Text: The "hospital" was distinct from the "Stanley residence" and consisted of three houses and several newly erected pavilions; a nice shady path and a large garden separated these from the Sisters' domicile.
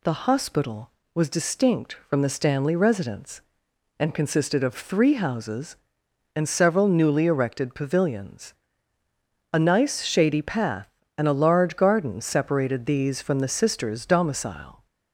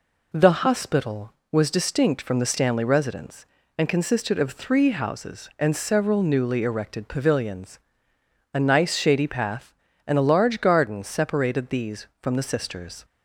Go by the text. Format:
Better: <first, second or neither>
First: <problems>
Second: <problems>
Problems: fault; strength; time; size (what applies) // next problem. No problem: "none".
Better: first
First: none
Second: stops before "domicile"; at 13.0 s